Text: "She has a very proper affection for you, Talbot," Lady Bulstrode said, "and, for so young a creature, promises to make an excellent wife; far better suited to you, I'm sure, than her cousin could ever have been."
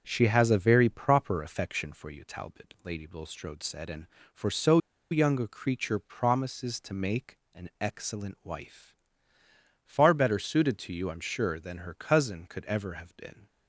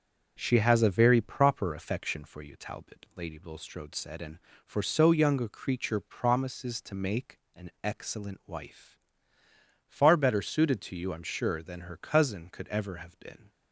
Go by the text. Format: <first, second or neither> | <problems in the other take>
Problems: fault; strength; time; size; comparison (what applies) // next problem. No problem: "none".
second | starts louder than the rest; until 1.0 s; 6.5 dB; also in the second // pauses between "so" and "young"; slight; at 4.7 s; 0.33 s long // pauses between "make" and "an"; slight; at 7.3 s; 0.16 s long; slight in the second